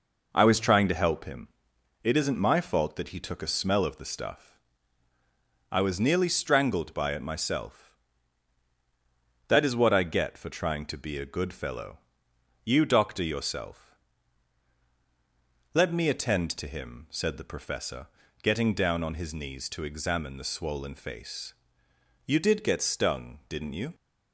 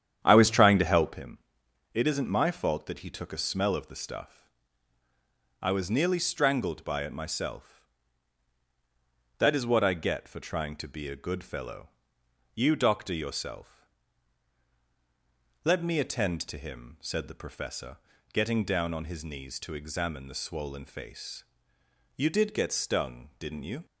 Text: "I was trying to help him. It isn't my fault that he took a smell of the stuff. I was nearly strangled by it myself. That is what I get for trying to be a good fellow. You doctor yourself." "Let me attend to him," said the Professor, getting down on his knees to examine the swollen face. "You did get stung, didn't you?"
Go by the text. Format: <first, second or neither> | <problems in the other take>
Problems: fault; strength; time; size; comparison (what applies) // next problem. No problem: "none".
first | starts louder than the rest; strong; until 1.2 s; 9.5 dB